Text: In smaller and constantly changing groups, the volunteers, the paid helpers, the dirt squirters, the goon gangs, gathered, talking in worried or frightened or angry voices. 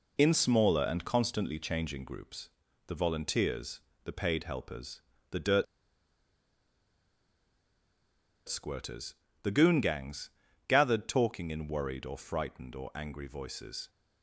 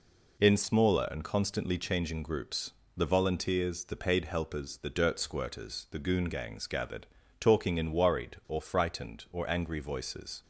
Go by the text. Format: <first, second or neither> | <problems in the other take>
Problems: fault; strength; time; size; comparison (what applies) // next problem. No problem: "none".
second | pauses between "dirt" and "squirters"; strong; at 5.6 s; 2.8 s long